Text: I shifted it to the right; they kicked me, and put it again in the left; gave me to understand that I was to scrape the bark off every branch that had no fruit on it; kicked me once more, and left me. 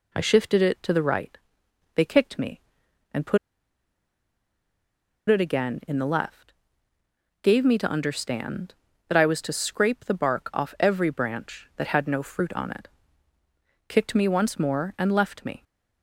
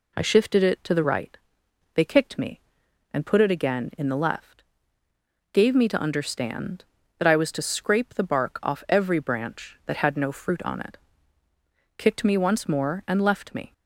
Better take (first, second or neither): second